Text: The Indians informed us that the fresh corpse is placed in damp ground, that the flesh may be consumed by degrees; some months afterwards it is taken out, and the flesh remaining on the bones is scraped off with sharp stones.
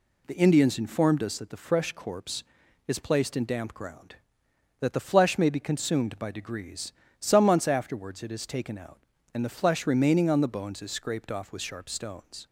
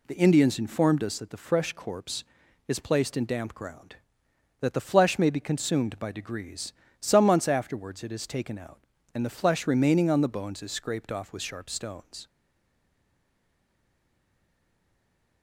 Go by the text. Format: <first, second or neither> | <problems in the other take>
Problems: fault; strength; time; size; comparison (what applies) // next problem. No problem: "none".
first | stays silent after the last word; strong; from 12.2 s on; 3.2 s long